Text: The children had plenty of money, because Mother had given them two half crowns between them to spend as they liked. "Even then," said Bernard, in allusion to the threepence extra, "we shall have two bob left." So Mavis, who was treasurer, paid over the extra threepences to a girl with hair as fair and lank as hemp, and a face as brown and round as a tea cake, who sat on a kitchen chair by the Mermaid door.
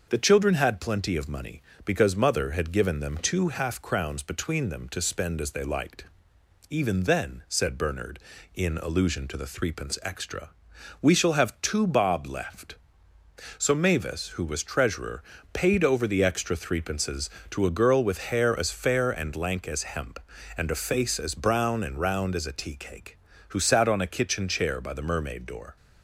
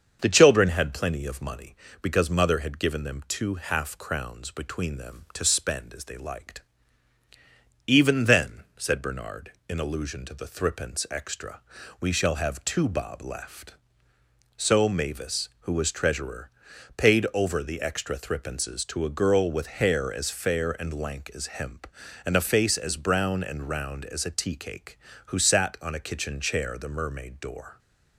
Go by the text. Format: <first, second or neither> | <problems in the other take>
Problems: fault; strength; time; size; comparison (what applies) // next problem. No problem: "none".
first | starts louder than the rest; until 1.2 s; 7 dB; also in the first // skips "by"; at 26.7 s